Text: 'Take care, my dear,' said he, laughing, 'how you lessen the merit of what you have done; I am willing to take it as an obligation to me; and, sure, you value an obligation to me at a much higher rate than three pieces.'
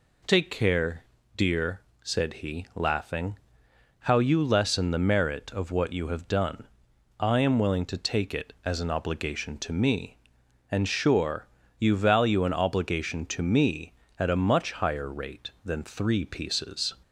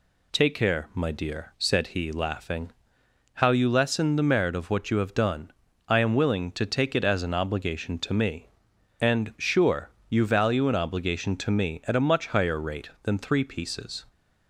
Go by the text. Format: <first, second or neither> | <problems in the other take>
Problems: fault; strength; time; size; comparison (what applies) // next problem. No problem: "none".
second | skips "my"; at 1.1 s